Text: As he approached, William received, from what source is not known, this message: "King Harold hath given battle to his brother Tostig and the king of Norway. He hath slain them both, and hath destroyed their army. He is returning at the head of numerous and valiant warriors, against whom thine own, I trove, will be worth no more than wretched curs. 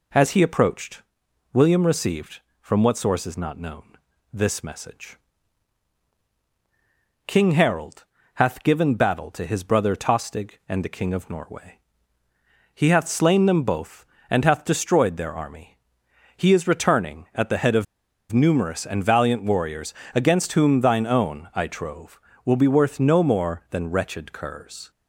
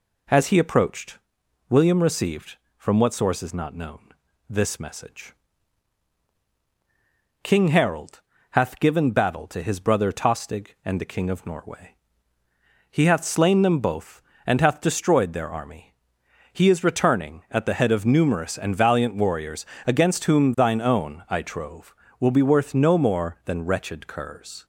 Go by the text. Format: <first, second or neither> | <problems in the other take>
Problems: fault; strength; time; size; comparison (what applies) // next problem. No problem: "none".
second | pauses between "Harold" and "hath"; slight; at 8.0 s; 0.30 s long; slight in the second // pauses between "of" and "numerous"; noticeable; at 17.8 s; 0.47 s long